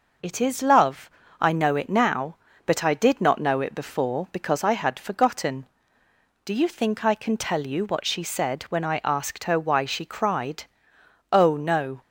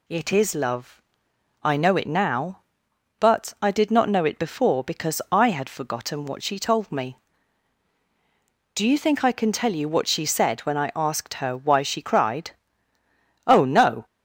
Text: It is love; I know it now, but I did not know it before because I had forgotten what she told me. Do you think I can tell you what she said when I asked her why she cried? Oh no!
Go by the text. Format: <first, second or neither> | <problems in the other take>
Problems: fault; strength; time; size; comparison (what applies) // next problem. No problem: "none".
second | skips "what she told me"; at 6.0 s